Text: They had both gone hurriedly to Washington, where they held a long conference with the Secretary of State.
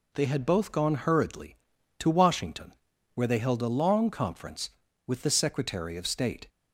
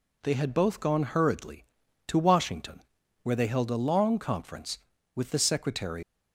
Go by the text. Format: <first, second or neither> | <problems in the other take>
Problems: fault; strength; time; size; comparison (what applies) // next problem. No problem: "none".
first | stops before "of State"; at 6.0 s